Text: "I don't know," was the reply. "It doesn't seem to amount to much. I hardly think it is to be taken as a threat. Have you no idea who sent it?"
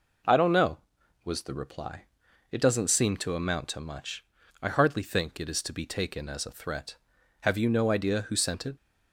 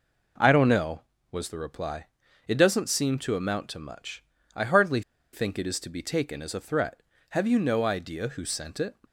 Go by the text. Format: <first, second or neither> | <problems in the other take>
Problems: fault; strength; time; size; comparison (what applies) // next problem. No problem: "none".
first | pauses between "hardly" and "think"; slight; at 5.0 s; 0.32 s long